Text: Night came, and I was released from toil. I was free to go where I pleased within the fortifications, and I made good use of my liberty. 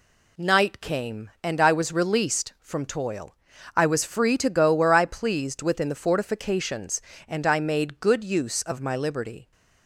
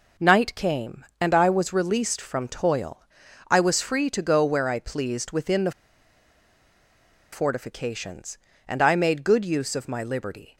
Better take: first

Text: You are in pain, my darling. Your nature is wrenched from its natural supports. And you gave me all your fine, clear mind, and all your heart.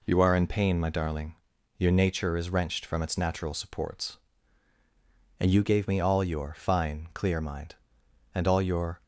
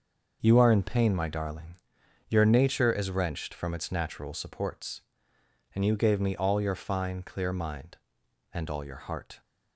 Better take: second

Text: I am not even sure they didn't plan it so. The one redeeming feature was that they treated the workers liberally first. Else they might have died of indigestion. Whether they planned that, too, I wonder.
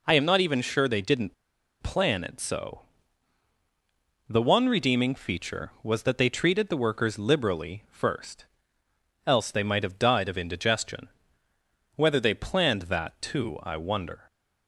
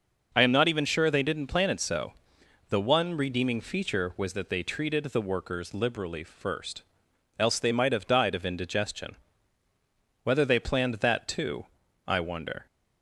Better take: second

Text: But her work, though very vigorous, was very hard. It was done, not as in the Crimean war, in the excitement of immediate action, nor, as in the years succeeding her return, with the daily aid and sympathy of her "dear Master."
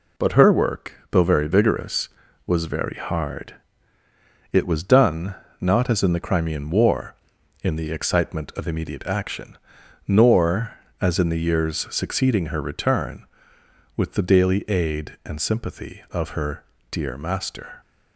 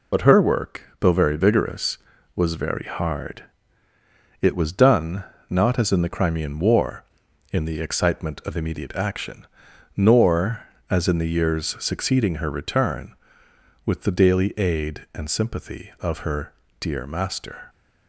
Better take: first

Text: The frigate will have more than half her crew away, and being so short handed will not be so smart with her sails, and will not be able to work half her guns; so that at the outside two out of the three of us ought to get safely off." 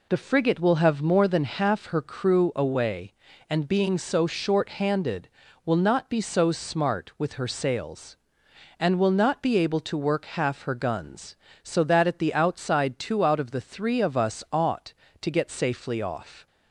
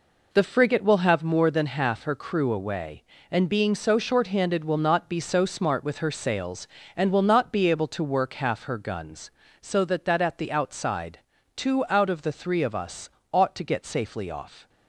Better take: first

